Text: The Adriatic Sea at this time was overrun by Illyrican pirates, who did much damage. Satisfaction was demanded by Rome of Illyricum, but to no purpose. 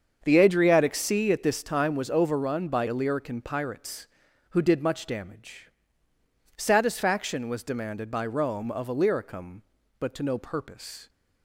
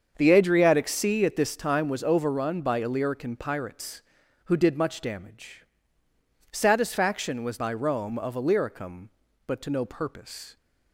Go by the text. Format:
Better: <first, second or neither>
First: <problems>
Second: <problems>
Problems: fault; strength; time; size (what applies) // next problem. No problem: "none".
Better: first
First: starts louder than the rest; until 1.2 s; 7 dB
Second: starts louder than the rest; until 1.1 s; 7 dB // skips "demanded"; at 7.5 s